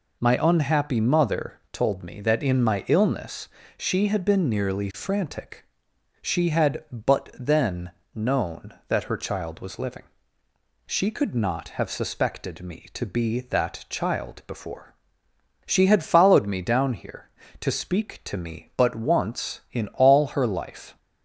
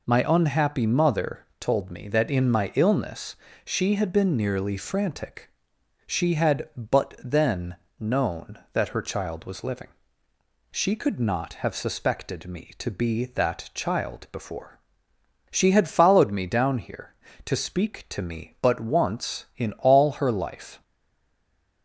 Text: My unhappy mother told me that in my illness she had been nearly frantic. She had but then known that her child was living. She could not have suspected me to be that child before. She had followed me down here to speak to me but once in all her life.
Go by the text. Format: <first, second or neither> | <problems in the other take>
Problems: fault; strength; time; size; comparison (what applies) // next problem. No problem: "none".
first | pauses between "mother" and "told"; slight; at 1.4 s; 0.15 s long // pauses between "illness" and "she"; slight; at 3.3 s; 0.28 s long; slight in the first // pauses between "then" and "known"; slight; at 7.7 s; 0.24 s long; slight in the first // stays silent after the last word; from 20.8 s on; 1.0 s long